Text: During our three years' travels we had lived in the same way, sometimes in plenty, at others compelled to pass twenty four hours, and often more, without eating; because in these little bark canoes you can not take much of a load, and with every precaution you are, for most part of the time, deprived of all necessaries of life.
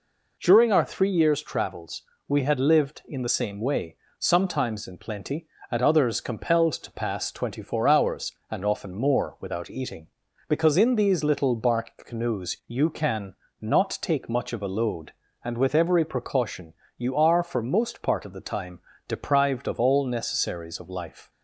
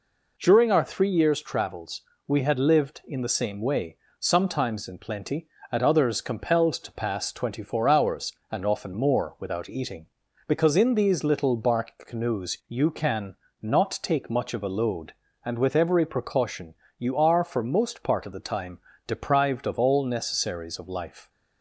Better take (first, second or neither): neither